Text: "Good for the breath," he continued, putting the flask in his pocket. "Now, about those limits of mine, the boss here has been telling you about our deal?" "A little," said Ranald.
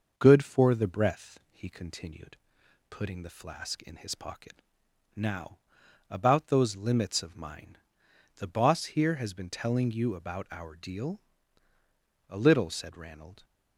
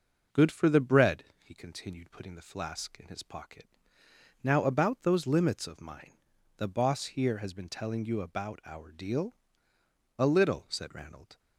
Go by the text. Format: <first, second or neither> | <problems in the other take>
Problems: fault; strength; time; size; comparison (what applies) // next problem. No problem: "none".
first | says "bread" for "breath"; at 0.8 s